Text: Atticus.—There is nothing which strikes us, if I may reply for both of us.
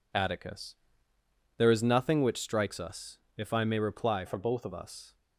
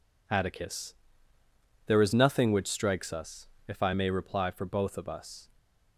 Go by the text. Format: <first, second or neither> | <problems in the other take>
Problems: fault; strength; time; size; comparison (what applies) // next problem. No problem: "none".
second | changes voice from "for" to "of"; from 4.2 to 4.7 s; 0.5 s long